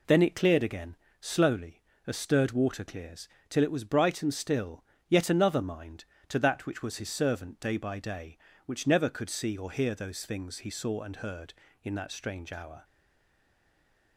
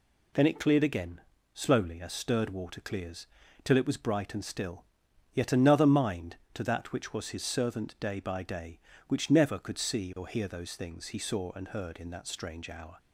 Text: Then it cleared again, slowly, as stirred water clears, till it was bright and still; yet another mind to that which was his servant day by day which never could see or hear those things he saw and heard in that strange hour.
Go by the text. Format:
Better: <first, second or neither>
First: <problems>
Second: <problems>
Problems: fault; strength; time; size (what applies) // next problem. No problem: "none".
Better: second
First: stays silent after the last word; noticeable; from 12.8 s on; 1.3 s long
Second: none